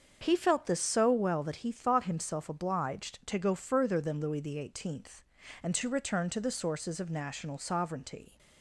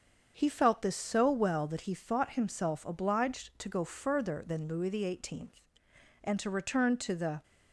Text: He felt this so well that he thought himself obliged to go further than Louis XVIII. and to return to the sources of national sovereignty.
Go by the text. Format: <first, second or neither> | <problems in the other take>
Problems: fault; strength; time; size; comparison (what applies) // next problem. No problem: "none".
first | starts louder than the rest; until 1.3 s; 7 dB; also in the first // stops before "sources of national sovereignty"; at 7.4 s